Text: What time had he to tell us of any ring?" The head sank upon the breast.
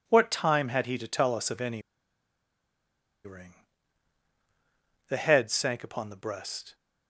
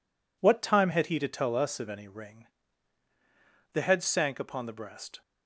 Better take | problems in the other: second | pauses between "any" and "ring"; strong; at 1.8 s; 1.4 s long

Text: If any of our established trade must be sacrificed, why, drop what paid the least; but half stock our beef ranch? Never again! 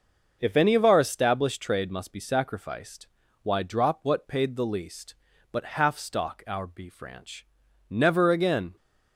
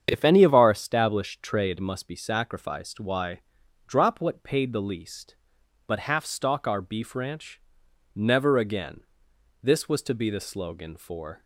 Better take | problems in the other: first | starts louder than the rest; strong; until 1.1 s; 8 dB // goes on to say "This was to be the slogan for"; strong; from 9.6 s on; 1.8 s long

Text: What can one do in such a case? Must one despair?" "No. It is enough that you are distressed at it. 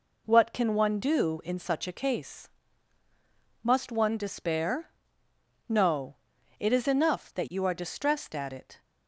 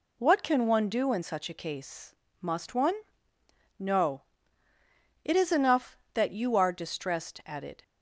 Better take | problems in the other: first | skips "despair"; at 3.3 s

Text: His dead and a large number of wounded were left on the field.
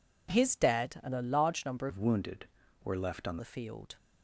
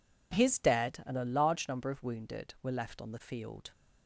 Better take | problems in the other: second | changes voice from "of" to "on"; from 1.8 to 3.3 s; 1.5 s long

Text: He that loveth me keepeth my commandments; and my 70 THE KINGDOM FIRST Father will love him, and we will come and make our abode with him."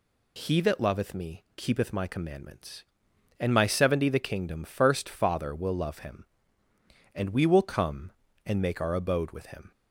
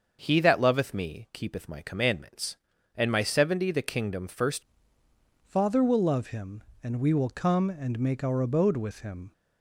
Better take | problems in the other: first | starts louder than the rest; until 1.2 s; 6.5 dB // changes voice at "Father"; from 5.4 s on; 3.9 s long

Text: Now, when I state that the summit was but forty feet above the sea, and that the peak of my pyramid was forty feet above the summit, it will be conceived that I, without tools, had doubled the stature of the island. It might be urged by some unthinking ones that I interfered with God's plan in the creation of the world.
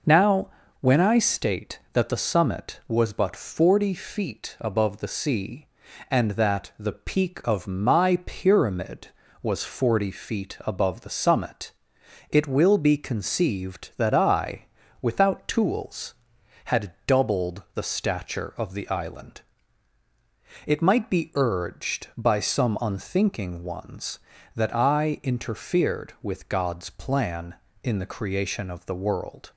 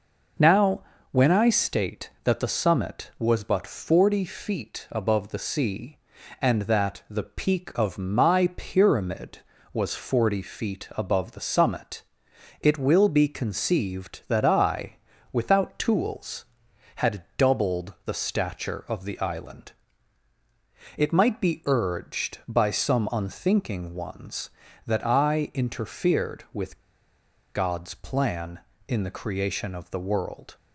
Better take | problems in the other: first | pauses between "with" and "God's"; noticeable; at 26.7 s; 0.75 s long

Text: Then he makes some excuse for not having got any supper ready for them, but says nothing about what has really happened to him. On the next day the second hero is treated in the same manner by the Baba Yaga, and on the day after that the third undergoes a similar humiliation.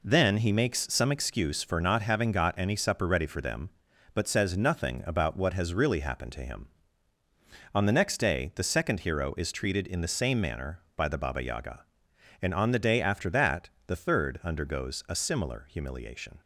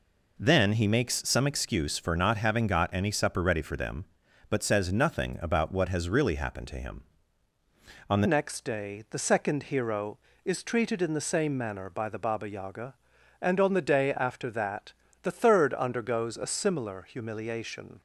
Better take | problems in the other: first | changes voice at "next"; from 8.2 s on; 9.8 s long // pauses between "that" and "the"; slight; at 14.9 s; 0.30 s long; slight in the first

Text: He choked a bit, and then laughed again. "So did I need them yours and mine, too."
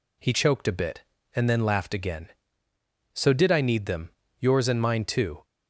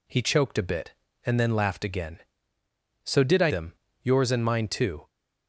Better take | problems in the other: first | skips "need"; at 3.5 s // pauses between "them" and "yours"; slight; at 3.7 s; 0.26 s long; slight in the first

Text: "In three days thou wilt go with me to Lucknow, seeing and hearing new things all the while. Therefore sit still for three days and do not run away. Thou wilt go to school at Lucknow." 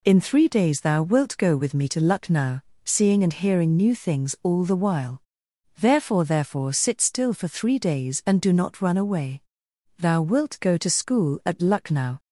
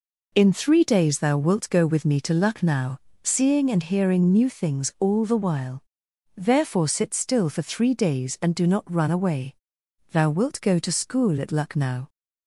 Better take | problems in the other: second | says "Therefore" twice; at 6.2 s

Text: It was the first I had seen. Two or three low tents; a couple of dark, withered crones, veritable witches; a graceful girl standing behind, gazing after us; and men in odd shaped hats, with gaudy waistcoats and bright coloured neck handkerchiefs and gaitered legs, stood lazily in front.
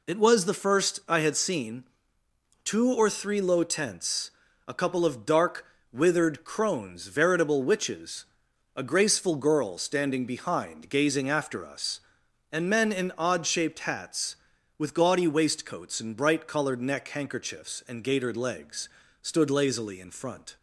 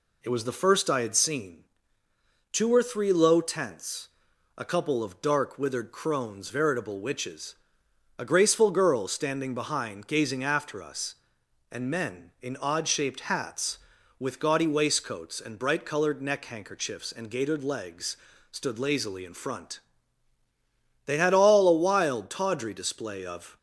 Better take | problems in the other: first | goes on to say "They had all a wild tawdry display of"; strong; from 21.0 s on; 2.5 s long

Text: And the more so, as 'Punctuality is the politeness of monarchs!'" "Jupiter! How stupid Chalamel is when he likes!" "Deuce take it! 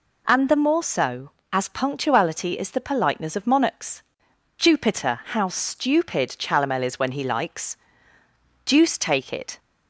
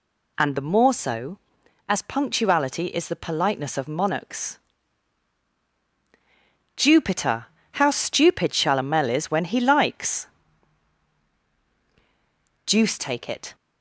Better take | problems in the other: neither | none

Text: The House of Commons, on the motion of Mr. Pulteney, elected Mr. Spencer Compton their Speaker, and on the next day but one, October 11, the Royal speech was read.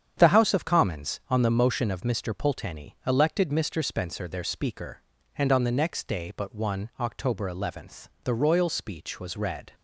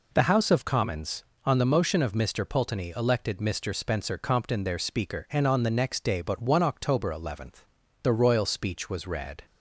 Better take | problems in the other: second | starts louder than the rest; strong; until 1.1 s; 8 dB // skips "Compton"; at 4.2 s

